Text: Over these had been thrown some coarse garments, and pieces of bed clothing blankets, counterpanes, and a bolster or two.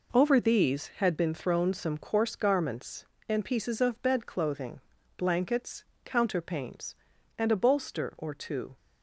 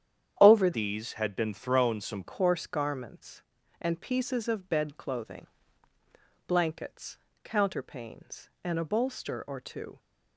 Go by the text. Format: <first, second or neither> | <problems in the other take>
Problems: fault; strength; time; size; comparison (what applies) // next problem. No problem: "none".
first | starts louder than the rest; strong; until 1.4 s; 9.5 dB // changes voice from "these" to "some"; from 0.7 to 2.2 s; 1.5 s long // pauses between "clothing" and "blankets"; at 5.4 s; 1.0 s long; slight in the first